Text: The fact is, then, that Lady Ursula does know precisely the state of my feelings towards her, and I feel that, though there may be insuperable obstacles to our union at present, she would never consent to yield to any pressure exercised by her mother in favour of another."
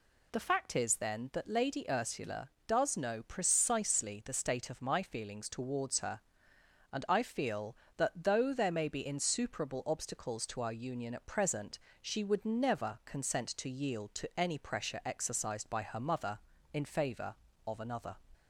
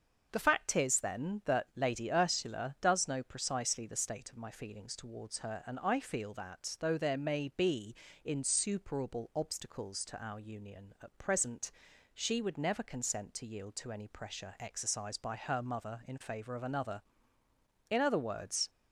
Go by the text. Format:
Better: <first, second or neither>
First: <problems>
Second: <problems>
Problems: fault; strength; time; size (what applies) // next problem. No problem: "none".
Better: first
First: none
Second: starts louder than the rest; until 1.3 s; 6.5 dB // pauses between "be" and "insuperable"; slight; at 7.9 s; 0.28 s long // goes on to say "In other words"; noticeable; from 17.8 s on; 0.80 s long